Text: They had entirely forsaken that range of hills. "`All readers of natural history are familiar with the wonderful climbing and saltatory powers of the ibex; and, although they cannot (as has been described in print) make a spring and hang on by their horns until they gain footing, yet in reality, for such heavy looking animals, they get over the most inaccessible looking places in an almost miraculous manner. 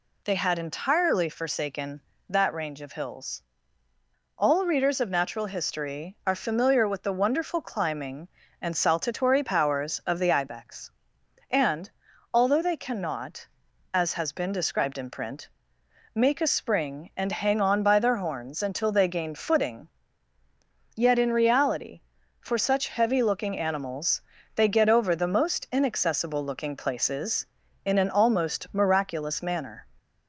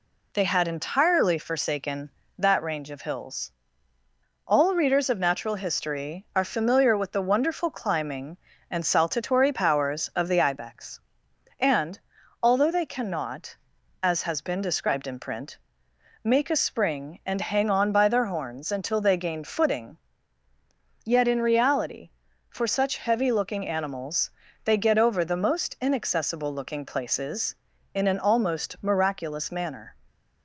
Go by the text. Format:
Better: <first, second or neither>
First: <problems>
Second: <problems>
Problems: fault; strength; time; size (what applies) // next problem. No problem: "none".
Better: first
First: none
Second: gets quieter; slight; throughout; 2 dB